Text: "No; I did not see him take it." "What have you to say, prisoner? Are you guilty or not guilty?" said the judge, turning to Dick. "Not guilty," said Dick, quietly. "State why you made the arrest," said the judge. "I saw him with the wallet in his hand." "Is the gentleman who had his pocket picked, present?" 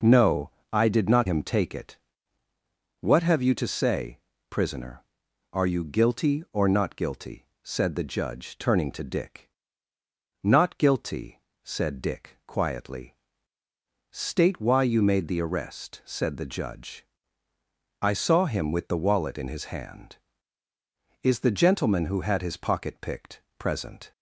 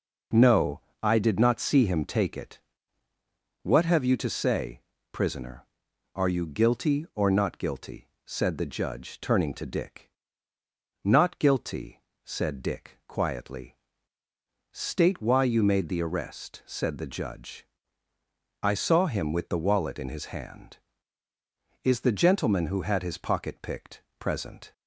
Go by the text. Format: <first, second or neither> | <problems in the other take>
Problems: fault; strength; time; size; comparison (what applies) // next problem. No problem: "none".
second | skips "see"; at 1.2 s